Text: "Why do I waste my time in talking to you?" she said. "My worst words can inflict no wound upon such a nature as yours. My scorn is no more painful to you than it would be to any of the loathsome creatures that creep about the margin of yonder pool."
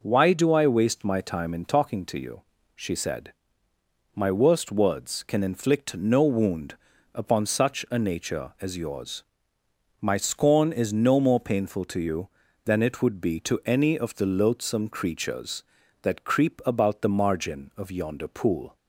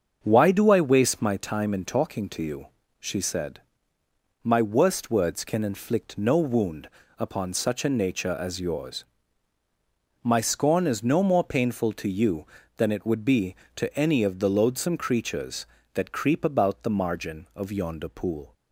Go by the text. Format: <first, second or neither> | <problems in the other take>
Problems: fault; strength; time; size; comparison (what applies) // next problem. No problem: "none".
first | starts louder than the rest; until 1.4 s; 6.5 dB // pauses between "wound" and "upon"; slight; at 6.8 s; 0.28 s long; also in the first